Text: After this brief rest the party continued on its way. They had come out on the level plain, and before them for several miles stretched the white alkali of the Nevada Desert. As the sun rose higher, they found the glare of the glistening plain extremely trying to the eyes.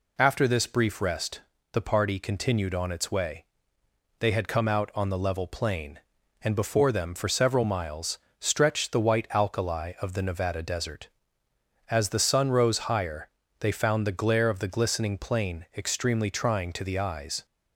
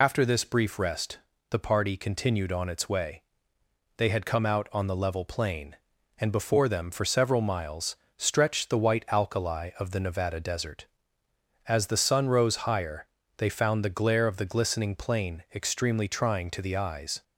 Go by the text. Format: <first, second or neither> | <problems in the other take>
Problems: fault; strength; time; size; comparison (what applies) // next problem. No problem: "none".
first | loses the start of "After"; at 0.0 s; 45 ms // pauses between "rest" and "the"; slight; at 1.1 s; 0.32 s long; slight in the first // pauses between "miles" and "stretched"; slight; at 7.9 s; 0.22 s long; slight in the first